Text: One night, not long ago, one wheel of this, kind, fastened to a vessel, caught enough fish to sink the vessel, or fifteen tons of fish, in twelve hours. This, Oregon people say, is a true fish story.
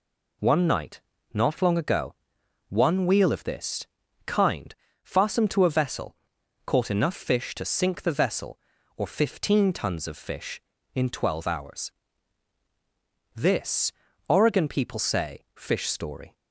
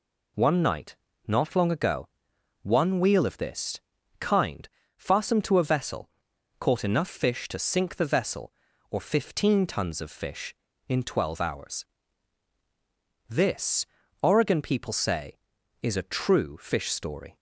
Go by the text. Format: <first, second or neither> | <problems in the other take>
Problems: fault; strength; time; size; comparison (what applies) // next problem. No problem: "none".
second | skips "is a true"; at 15.5 s